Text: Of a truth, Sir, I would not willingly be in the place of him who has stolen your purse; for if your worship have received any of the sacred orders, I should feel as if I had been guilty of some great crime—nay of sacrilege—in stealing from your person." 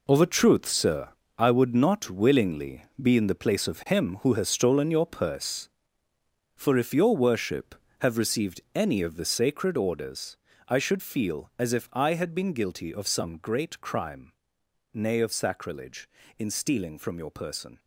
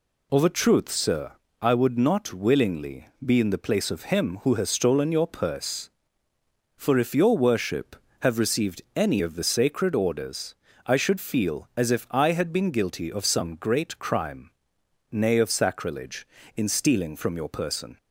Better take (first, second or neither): second